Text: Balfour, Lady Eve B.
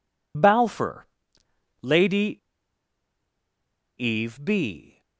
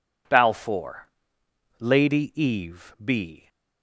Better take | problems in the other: second | pauses between "Lady" and "Eve"; strong; at 2.3 s; 1.6 s long

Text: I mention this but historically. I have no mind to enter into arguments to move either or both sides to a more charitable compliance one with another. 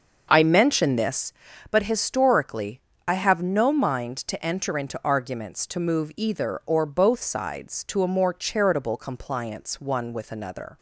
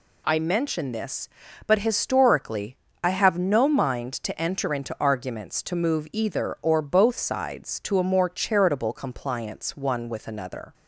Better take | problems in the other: second | starts louder than the rest; until 1.3 s; 6.5 dB

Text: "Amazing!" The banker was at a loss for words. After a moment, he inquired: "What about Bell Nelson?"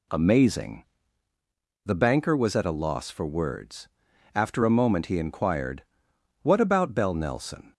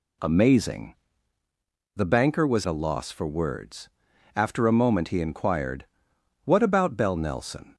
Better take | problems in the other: first | skips "at"; at 2.6 s

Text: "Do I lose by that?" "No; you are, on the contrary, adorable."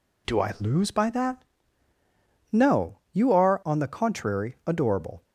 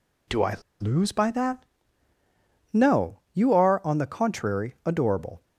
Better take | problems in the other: first | pauses between "I" and "lose"; slight; at 0.5 s; 0.24 s long

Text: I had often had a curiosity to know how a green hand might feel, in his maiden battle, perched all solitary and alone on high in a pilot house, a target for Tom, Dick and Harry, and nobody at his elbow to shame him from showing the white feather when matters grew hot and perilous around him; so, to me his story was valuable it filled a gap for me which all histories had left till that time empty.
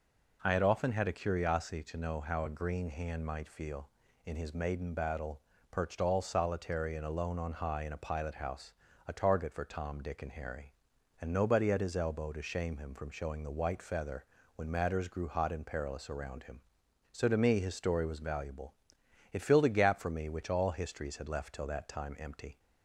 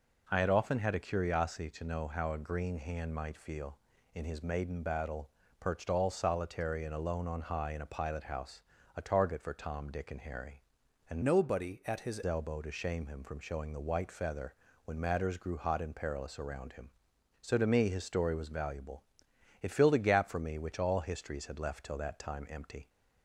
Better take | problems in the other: first | changes voice from "nobody" to "his"; from 11.2 to 12.2 s; 1.0 s long // pauses between "feather" and "when"; slight; at 14.5 s; 0.28 s long; slight in the first // pauses between "valuable" and "it"; noticeable; at 19.0 s; 0.58 s long; noticeable in the first

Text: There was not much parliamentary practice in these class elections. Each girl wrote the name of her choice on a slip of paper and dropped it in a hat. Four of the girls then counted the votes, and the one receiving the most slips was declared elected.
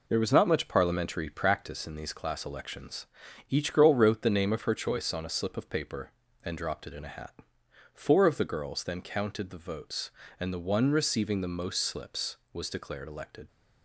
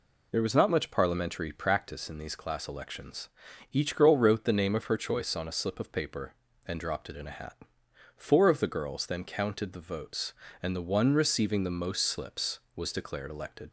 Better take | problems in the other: second | gets quieter; noticeable; throughout; 5.5 dB

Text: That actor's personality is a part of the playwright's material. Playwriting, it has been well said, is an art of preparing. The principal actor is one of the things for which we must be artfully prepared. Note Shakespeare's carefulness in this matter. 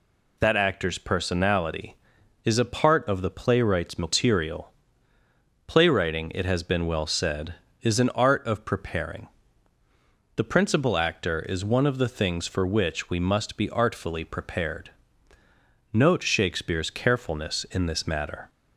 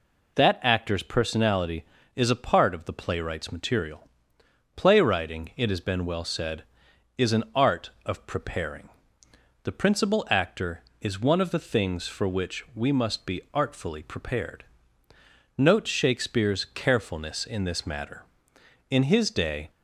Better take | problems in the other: first | goes on to say "In his day"; noticeable; from 18.8 s on; 0.80 s long

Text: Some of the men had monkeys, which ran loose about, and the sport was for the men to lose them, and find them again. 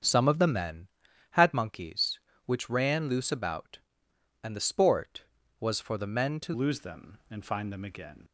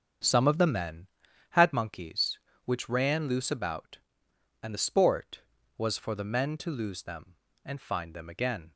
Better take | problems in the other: second | starts louder than the rest; strong; until 1.4 s; 8 dB; strong in the second // changes voice at "lose"; from 6.5 s on; 1.7 s long

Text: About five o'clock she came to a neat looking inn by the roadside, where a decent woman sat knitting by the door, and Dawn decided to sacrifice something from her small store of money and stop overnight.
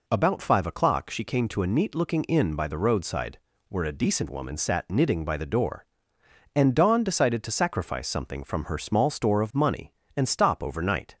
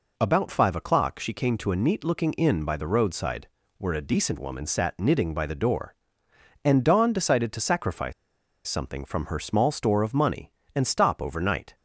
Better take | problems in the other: first | pauses between "sacrifice" and "something"; noticeable; at 8.1 s; 0.54 s long

